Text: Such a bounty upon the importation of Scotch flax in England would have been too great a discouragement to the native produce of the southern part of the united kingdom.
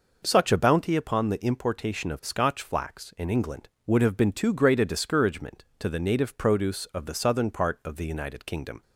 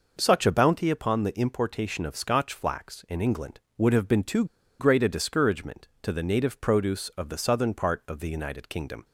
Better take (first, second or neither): first